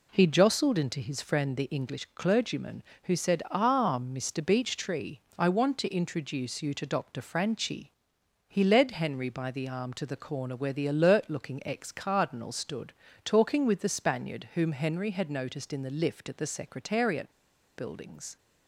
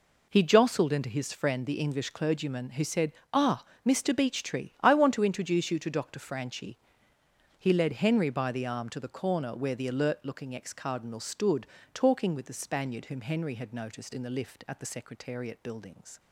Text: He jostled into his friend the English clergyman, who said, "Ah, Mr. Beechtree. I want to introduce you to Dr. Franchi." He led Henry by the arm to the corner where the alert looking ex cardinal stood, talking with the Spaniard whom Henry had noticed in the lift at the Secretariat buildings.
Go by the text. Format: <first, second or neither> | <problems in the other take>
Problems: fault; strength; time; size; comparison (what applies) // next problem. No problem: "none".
second | pauses between "Secretariat" and "buildings"; noticeable; at 17.3 s; 0.46 s long